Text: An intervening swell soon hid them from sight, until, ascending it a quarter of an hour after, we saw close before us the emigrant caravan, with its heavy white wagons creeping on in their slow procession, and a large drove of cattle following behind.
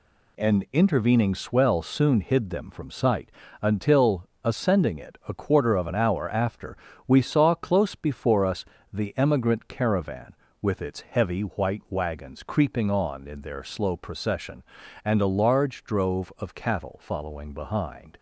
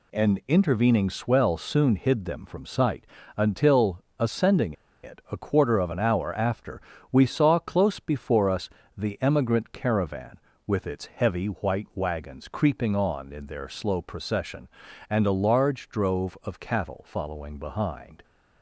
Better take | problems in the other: first | pauses between "ascending" and "it"; slight; at 4.7 s; 0.31 s long // pauses between "us" and "the"; slight; at 8.6 s; 0.28 s long; slight in the first

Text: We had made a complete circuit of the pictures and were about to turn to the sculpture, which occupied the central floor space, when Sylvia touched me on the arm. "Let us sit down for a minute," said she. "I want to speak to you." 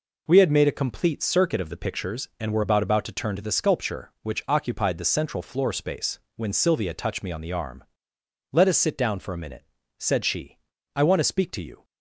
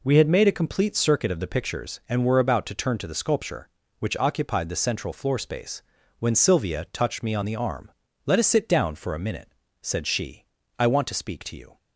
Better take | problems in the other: second | says "about" twice; at 2.8 s

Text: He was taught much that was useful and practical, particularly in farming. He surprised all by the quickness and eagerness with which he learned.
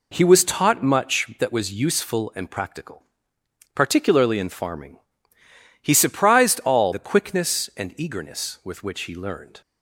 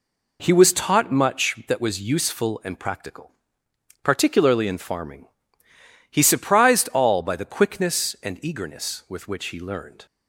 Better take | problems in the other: second | skips "by"; at 6.9 s

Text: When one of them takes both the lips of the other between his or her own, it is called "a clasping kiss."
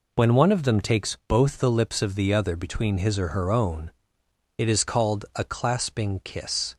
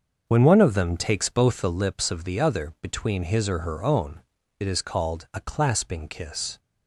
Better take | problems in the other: first | starts louder than the rest; until 1.8 s; 6.5 dB

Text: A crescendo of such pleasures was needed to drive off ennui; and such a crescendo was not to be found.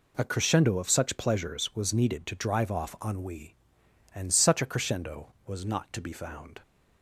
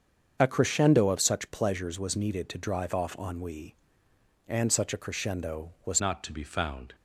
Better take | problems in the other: first | starts louder than the rest; until 1.4 s; 7 dB // changes voice at "not"; from 6.0 s on; 0.9 s long

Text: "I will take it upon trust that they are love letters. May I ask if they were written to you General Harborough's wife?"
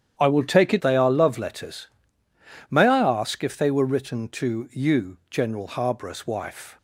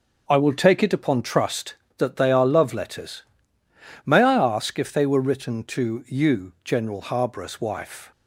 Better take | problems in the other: second | starts louder than the rest; strong; until 1.1 s; 9 dB // skips "upon trust that"; at 0.8 s

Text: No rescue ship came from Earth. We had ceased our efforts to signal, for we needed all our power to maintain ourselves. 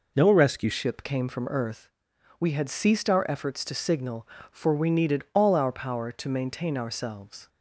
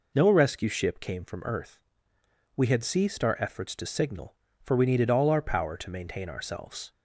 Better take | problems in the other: second | changes voice at "ship"; from 0.7 s on; 6.7 s long

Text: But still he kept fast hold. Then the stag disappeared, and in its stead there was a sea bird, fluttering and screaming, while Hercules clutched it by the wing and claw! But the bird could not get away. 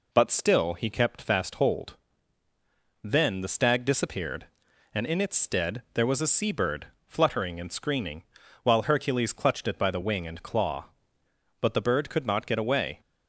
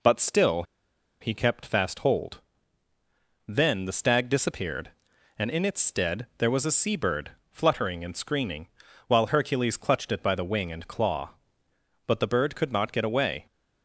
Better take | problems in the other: first | pauses between "still" and "he"; noticeable; at 0.6 s; 0.58 s long

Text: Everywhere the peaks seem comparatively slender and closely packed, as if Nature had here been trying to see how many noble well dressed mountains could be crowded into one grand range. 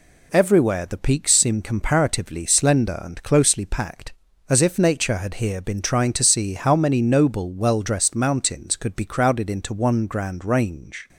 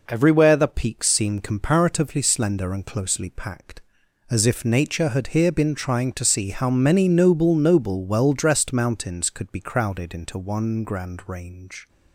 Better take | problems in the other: first | says "noble" twice; at 7.5 s

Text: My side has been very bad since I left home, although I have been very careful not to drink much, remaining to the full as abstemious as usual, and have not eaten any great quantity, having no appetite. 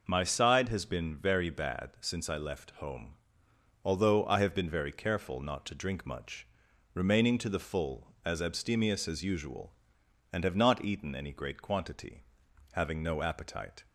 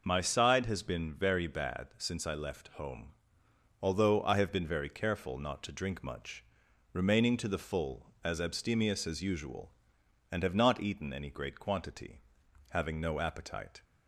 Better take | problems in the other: neither | none

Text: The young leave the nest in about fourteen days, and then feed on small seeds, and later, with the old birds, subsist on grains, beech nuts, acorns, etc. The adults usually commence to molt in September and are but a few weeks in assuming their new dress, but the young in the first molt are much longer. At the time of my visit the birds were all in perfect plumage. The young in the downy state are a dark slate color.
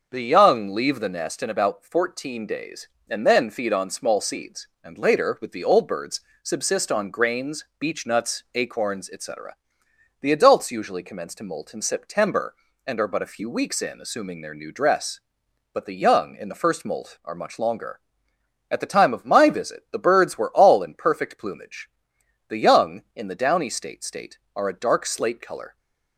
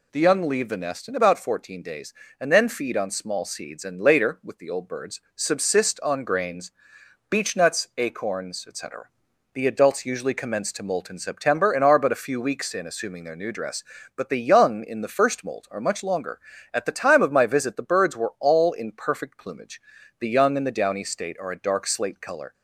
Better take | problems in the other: second | starts louder than the rest; noticeable; until 1.1 s; 6 dB // says "state" twice; at 24.0 s

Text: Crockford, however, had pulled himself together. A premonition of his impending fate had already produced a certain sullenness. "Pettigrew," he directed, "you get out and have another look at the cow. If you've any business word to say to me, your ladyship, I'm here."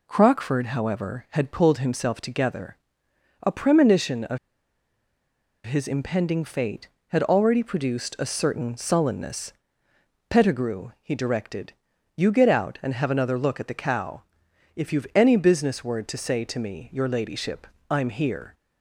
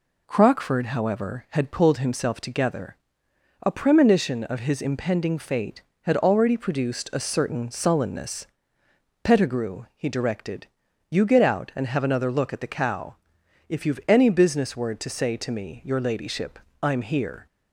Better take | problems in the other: second | pauses between "of" and "his"; strong; at 4.3 s; 1.2 s long

